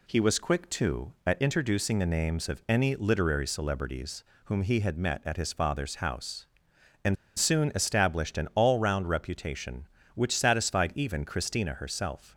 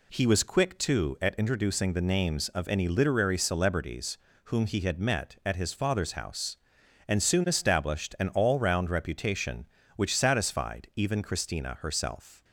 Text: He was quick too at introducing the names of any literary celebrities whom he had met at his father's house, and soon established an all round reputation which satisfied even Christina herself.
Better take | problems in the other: second | pauses between "celebrities" and "whom"; slight; at 4.2 s; 0.22 s long; slight in the second // pauses between "and" and "soon"; slight; at 7.1 s; 0.22 s long

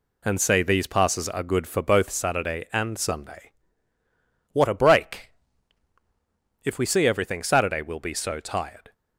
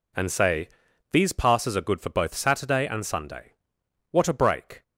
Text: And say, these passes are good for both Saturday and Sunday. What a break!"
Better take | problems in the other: second | goes on to say "If we see everything Saturday we'll be so tired"; strong; from 6.6 s on; 2.3 s long

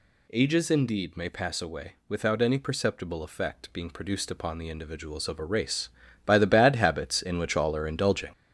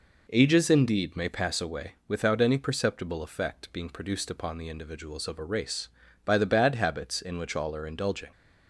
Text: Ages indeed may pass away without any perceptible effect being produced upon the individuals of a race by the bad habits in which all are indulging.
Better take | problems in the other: second | gets louder; noticeable; throughout; 5.5 dB

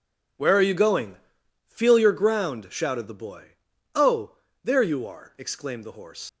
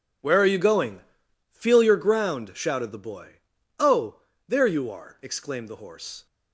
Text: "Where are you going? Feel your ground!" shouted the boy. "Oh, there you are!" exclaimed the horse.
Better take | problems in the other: second | leaves "horse" unfinished; at 6.2 s; 125 ms

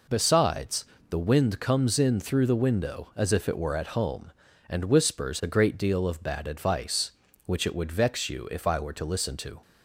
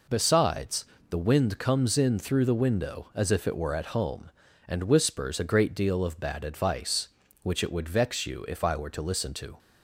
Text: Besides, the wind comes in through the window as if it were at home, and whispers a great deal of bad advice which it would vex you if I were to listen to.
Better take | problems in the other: neither | none

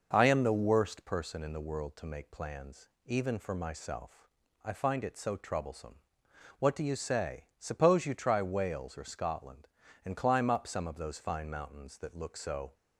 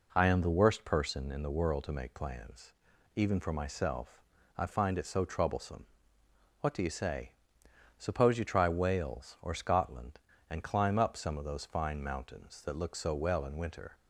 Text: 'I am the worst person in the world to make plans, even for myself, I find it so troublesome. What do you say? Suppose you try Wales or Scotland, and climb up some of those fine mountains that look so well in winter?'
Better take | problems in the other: second | stops before "well in winter"; at 12.7 s

